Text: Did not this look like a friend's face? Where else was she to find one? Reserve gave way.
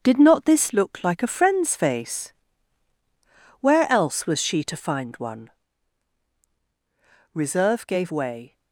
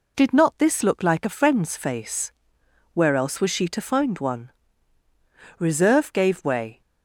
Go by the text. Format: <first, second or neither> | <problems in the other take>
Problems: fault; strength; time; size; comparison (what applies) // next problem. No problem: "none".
second | gets quieter; throughout; 6.5 dB